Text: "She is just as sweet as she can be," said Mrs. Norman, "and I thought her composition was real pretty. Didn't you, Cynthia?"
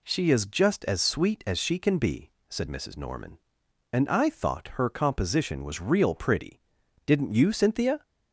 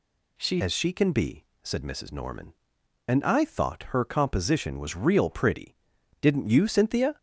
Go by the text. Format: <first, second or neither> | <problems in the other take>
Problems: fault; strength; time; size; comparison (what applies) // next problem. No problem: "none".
first | skips "is just as sweet"; at 0.6 s